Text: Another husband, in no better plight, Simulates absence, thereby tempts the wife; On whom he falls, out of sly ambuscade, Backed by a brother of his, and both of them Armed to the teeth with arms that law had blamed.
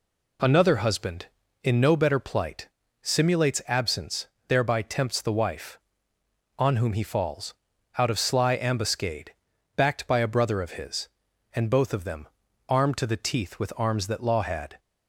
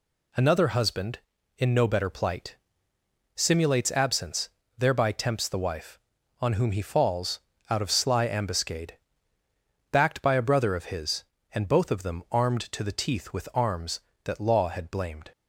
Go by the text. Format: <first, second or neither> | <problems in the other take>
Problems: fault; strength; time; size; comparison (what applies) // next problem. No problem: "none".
second | pauses between "them" and "Armed"; at 12.2 s; 0.42 s long // stops before "blamed"; at 14.7 s